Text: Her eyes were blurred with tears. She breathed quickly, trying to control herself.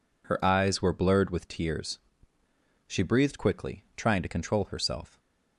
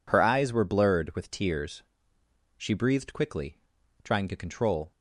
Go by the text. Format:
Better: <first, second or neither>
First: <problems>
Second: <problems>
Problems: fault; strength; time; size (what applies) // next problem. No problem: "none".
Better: first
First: none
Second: stops before "herself"; at 4.9 s